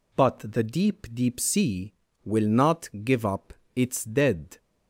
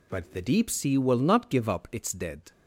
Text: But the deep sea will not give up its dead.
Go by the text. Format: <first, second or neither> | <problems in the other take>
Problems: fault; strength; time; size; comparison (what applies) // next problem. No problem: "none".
second | says "deep" twice; at 1.1 s // pauses between "up" and "its"; slight; at 3.5 s; 0.20 s long